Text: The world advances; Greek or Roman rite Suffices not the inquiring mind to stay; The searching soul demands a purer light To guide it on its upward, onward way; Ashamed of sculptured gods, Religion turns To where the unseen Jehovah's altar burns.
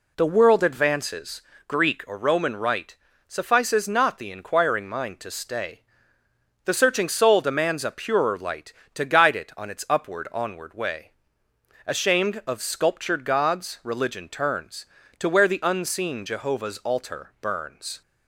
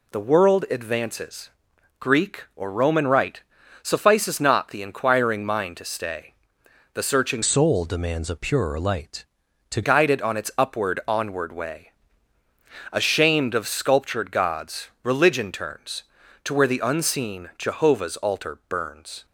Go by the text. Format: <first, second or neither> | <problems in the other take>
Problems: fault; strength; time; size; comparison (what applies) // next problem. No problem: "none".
first | pauses between "rite" and "Suffices"; at 3.4 s; 0.40 s long; slight in the first // changes voice from "soul" to "To"; from 7.4 to 9.8 s; 2.4 s long